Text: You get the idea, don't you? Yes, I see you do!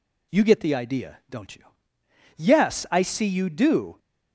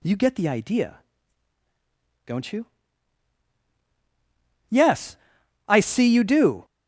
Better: neither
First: none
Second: none

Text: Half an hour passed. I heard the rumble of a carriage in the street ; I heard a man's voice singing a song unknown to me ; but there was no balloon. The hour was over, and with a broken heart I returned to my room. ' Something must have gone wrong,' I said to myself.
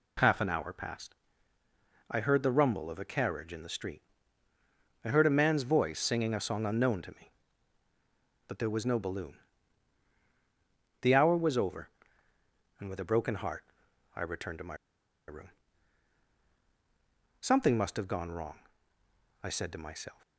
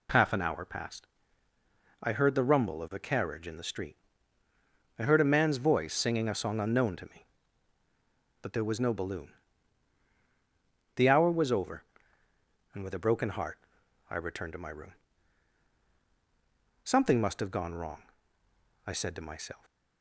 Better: second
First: pauses between "heart" and "I"; noticeable; at 13.6 s; 0.54 s long // pauses between "my" and "room"; noticeable; at 14.7 s; 0.53 s long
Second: pauses between "heart" and "I"; noticeable; at 13.5 s; 0.54 s long

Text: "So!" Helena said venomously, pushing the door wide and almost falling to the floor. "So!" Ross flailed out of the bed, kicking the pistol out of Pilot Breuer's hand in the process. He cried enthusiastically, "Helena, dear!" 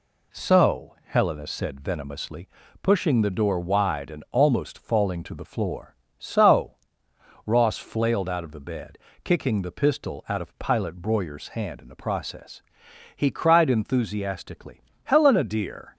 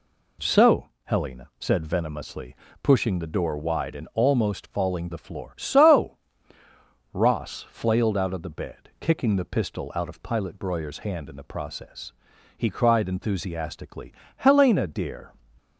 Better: first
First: none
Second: skips "to"; at 5.1 s

